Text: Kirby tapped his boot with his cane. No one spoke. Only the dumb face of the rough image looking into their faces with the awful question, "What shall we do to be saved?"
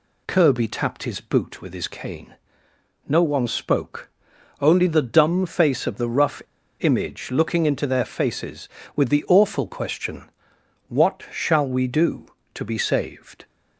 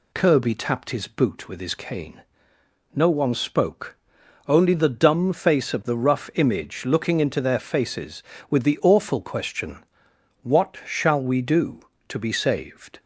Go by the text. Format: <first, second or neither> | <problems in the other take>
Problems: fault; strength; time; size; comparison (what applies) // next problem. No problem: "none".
second | pauses between "rough" and "image"; at 6.4 s; 0.39 s long